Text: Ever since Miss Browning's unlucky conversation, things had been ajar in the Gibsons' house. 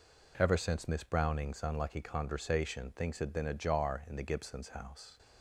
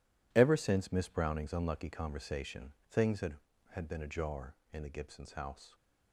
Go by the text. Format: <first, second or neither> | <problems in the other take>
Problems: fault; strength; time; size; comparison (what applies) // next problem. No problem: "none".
first | says "had" twice; at 3.7 s